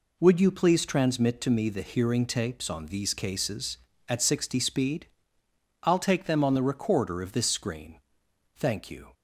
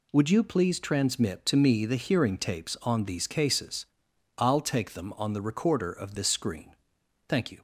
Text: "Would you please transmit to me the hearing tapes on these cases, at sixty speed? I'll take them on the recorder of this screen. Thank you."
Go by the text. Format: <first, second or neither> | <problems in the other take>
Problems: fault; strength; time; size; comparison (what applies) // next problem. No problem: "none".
first | skips "at sixty speed"; at 4.1 s